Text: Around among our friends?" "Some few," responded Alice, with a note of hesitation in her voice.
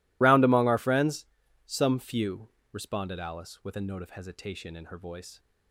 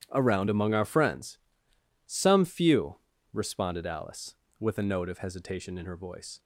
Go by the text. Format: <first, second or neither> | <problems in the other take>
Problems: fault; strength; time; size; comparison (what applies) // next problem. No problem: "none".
second | loses the start of "Around"; at 0.2 s; 110 ms